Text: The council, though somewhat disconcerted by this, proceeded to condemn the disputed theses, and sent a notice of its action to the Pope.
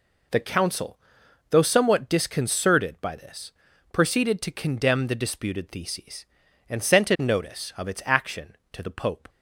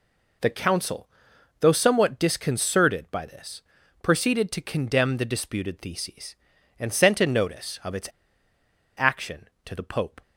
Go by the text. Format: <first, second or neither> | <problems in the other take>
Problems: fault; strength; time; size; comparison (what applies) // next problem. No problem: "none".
first | pauses between "its" and "action"; noticeable; at 8.0 s; 0.87 s long